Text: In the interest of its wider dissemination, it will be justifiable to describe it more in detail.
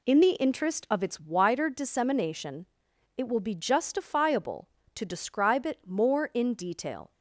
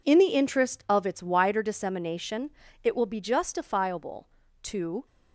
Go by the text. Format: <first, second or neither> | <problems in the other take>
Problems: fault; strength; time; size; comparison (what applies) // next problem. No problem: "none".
first | stops before "describe it more in detail"; at 5.0 s